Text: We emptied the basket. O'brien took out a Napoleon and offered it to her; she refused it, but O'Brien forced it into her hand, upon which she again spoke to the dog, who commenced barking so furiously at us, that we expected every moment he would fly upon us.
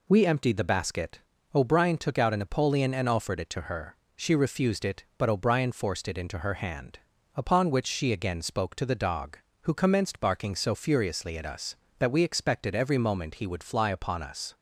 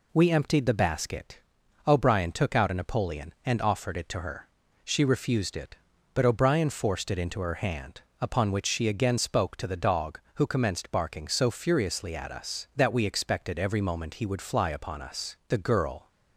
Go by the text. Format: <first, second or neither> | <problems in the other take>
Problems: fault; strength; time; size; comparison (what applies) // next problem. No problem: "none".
first | goes on to say "The girl"; from 15.4 s on; 0.58 s long